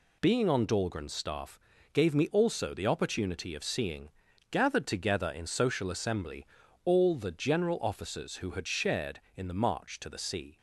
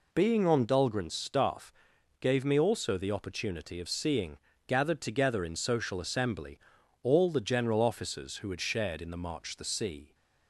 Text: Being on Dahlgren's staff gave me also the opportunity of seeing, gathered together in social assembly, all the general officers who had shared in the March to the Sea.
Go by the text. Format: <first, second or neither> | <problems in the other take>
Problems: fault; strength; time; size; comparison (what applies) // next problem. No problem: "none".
first | pauses between "staff" and "gave"; noticeable; at 1.7 s; 0.48 s long; slight in the first // skips "to"; at 9.5 s